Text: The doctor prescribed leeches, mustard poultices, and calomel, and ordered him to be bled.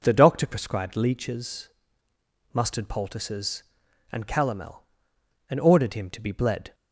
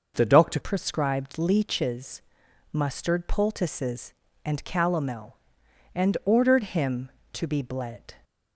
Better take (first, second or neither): first